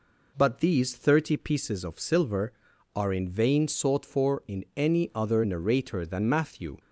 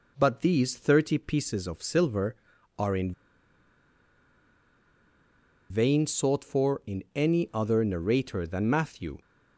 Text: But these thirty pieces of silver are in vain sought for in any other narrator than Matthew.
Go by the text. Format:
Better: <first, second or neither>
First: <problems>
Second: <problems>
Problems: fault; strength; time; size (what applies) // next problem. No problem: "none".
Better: first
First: none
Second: pauses between "in" and "vain"; strong; at 3.1 s; 2.5 s long